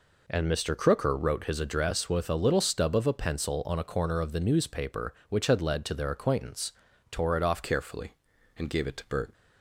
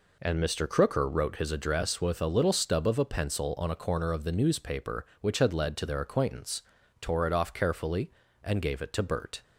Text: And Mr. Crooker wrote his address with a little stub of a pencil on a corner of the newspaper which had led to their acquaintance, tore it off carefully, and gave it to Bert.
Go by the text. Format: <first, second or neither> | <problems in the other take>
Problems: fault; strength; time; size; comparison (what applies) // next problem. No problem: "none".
second | changes voice at "carefully"; from 7.6 s on; 1.7 s long